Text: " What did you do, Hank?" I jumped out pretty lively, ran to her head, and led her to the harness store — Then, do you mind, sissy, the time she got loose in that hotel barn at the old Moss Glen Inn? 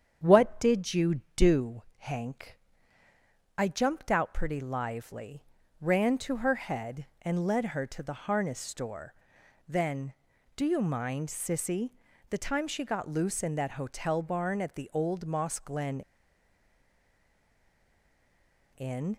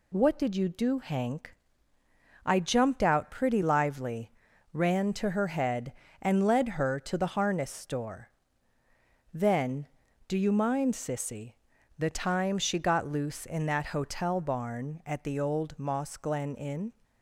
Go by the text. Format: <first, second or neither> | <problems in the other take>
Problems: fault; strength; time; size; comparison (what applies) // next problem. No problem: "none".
second | starts louder than the rest; strong; until 1.2 s; 8 dB // pauses between "Glen" and "Inn"; strong; at 16.0 s; 2.7 s long